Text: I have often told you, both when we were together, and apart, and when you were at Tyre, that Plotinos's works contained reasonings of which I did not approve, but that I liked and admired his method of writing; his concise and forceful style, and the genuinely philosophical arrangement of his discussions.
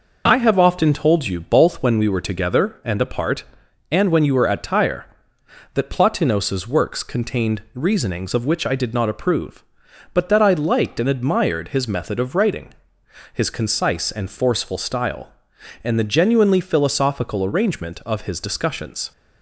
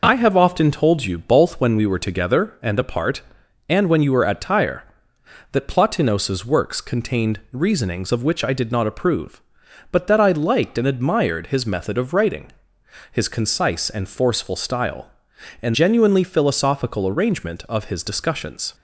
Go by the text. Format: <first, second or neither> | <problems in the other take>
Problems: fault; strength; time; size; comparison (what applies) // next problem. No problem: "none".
first | skips "the"; at 15.7 s